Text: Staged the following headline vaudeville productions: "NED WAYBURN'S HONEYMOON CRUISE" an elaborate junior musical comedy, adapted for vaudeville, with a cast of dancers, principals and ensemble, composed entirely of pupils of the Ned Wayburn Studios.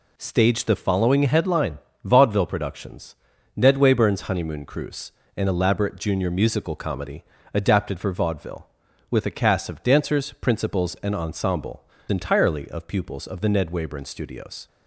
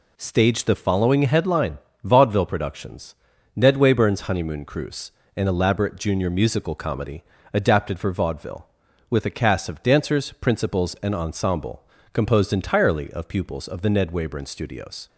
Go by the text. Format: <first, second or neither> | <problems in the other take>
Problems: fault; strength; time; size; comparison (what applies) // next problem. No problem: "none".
second | pauses between "headline" and "vaudeville"; slight; at 1.7 s; 0.24 s long; slight in the second // pauses between "CRUISE" and "an"; slight; at 5.1 s; 0.24 s long; slight in the second // skips "composed"; at 11.9 s